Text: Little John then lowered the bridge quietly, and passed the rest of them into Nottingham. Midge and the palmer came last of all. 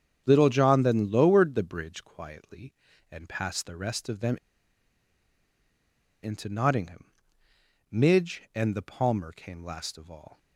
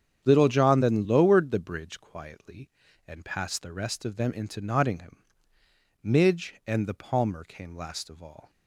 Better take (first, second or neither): second